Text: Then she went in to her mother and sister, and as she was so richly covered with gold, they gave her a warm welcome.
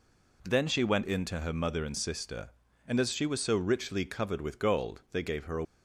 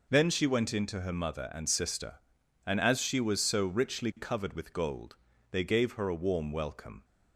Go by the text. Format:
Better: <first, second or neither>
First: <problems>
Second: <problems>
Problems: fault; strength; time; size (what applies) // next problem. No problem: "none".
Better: second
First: stops before "warm welcome"; at 5.6 s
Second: none